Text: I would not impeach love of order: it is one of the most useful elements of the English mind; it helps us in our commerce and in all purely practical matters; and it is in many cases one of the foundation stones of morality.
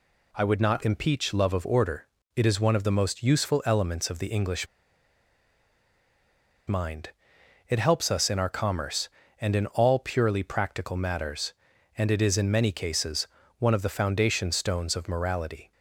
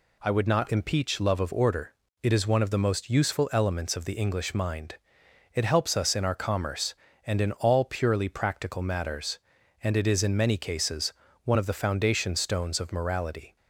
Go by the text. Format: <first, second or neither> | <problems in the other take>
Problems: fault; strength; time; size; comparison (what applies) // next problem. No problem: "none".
second | pauses between "English" and "mind"; strong; at 4.6 s; 2.0 s long // pauses between "cases" and "one"; slight; at 13.2 s; 0.32 s long; slight in the second